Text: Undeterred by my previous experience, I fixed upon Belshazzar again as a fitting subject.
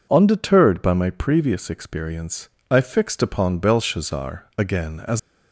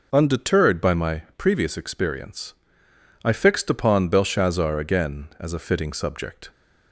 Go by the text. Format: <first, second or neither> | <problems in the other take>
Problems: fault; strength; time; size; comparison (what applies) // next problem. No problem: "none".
second | stops before "a fitting subject"; at 5.1 s